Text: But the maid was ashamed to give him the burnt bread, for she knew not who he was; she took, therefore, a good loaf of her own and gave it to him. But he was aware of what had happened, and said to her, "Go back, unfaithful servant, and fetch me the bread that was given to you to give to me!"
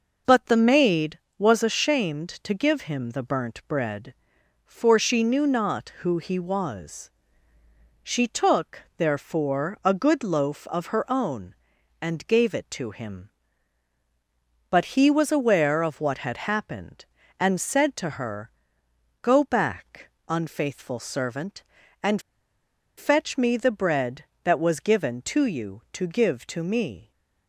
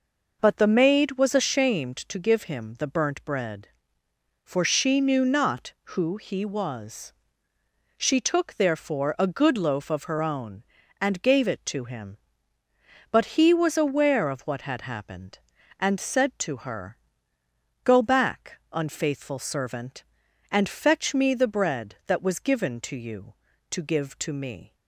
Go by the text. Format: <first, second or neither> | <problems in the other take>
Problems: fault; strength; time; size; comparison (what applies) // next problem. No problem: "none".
second | pauses between "and" and "fetch"; noticeable; at 22.1 s; 0.78 s long